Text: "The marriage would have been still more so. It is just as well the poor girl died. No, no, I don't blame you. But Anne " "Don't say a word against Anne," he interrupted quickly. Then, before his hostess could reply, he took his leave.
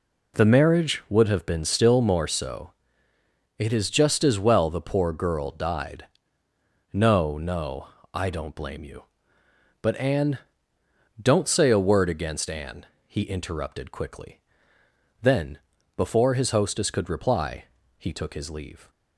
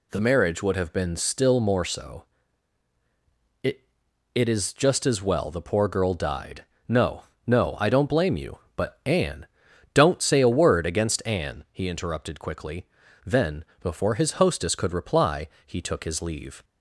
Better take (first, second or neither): first